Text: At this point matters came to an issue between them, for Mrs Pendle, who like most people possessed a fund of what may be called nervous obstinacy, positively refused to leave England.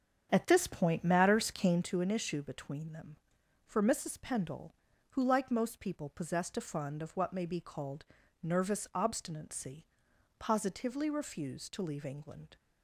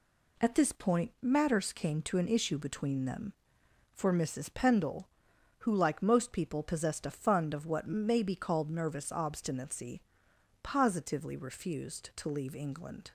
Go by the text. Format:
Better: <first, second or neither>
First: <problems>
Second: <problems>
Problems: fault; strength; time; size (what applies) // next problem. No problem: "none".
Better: second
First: starts louder than the rest; strong; until 1.9 s; 8 dB // pauses between "called" and "nervous"; slight; at 8.0 s; 0.36 s long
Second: none